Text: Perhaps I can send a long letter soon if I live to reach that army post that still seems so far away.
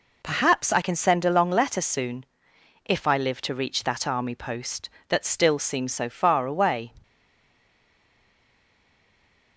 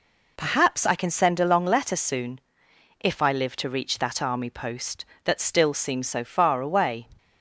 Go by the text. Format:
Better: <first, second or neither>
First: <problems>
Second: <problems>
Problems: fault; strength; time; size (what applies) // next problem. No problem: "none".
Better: second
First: pauses between "soon" and "if"; noticeable; at 2.2 s; 0.60 s long // stays silent after the last word; from 7.0 s on; 2.5 s long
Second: pauses between "soon" and "if"; noticeable; at 2.3 s; 0.60 s long